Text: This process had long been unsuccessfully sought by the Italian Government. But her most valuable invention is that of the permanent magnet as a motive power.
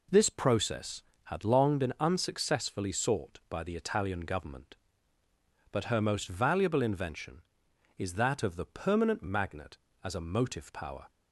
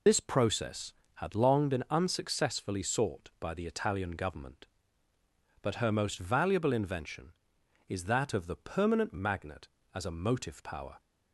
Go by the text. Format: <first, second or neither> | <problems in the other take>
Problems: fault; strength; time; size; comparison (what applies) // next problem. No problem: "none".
first | loses the start of "This"; at 0.0 s; 70 ms